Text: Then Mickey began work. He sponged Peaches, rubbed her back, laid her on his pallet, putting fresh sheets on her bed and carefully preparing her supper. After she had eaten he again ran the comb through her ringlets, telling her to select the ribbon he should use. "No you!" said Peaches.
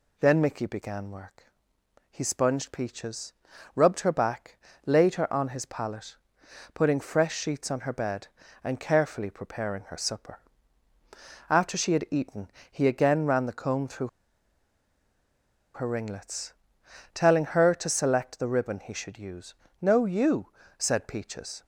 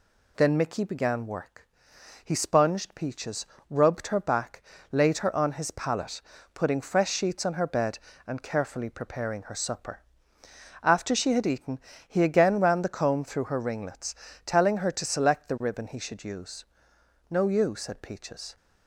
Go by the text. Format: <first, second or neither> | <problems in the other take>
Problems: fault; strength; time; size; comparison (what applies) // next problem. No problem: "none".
second | pauses between "eaten" and "he"; slight; at 12.4 s; 0.22 s long; slight in the second // pauses between "through" and "her"; strong; at 14.0 s; 1.6 s long